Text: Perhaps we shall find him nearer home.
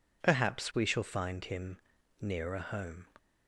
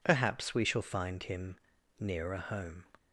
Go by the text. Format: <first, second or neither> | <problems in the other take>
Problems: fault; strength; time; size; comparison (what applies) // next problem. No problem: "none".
neither | pauses between "him" and "nearer"; the same in both